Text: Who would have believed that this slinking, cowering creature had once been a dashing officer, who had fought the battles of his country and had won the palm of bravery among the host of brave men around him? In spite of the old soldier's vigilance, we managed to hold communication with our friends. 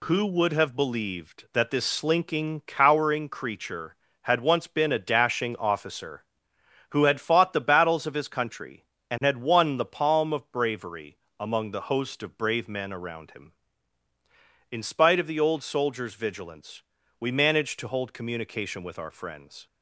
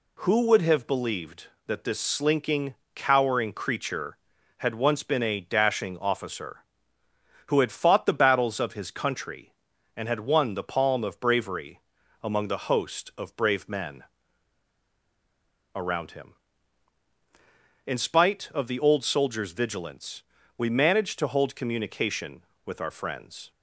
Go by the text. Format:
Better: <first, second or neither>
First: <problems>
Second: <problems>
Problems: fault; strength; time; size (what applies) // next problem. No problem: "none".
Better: first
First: pauses between "bravery" and "among"; slight; at 11.1 s; 0.24 s long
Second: pauses between "bravery" and "among"; at 11.8 s; 0.38 s long // pauses between "men" and "around"; strong; at 14.0 s; 1.7 s long